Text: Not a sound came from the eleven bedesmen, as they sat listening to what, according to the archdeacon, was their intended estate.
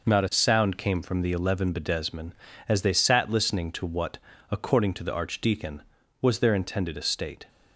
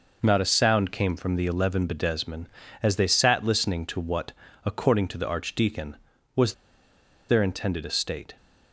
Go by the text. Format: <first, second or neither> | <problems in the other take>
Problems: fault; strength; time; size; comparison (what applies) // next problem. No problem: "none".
first | pauses between "was" and "their"; noticeable; at 6.5 s; 0.77 s long